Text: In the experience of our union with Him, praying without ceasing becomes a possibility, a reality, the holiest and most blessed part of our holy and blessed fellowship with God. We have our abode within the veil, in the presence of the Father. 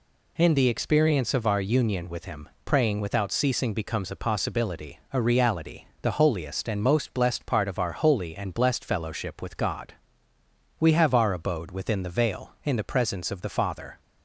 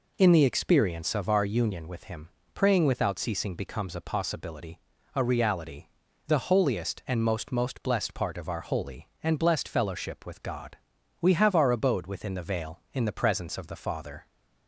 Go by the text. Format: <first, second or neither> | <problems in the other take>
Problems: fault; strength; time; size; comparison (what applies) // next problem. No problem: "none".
first | says "most" twice; at 7.5 s